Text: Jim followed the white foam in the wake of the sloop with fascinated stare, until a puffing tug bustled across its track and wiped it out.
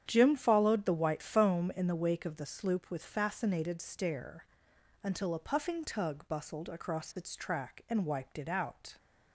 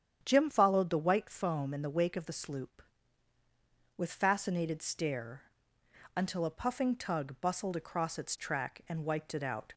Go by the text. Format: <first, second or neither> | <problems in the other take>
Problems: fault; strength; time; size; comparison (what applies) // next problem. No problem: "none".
neither | starts louder than the rest; strong; the same in both